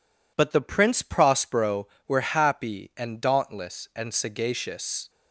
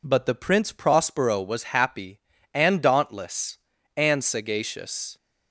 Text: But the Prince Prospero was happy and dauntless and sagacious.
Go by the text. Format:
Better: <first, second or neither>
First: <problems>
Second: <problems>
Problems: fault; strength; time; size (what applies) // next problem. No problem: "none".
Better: second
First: says "were" for "was"; at 2.0 s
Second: none